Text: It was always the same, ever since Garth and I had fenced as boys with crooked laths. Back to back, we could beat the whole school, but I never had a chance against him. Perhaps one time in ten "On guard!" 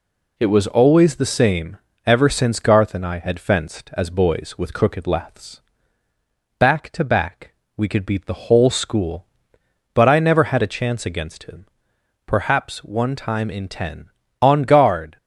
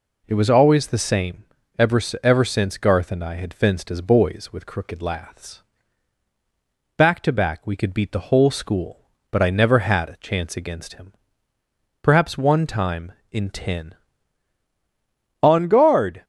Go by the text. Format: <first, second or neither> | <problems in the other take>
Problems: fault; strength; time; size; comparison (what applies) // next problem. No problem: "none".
first | says "ever" twice; at 2.2 s